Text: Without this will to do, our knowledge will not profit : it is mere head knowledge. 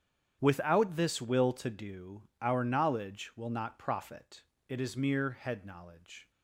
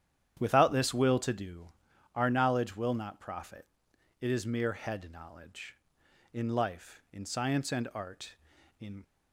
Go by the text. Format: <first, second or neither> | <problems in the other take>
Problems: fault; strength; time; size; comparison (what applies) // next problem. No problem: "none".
first | starts louder than the rest; strong; until 1.4 s; 10 dB; strong in the first // goes on to say "In life in science and art in"; strong; from 6.3 s on; 2.7 s long